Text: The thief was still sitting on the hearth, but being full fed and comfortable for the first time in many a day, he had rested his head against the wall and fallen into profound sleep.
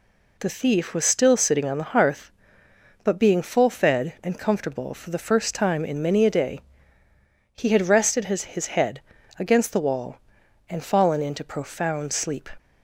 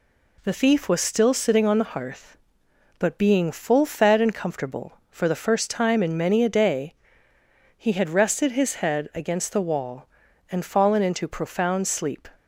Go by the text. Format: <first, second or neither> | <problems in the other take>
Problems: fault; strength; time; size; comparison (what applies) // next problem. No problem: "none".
second | says "his" twice; at 8.4 s // pauses between "head" and "against"; at 9.0 s; 0.38 s long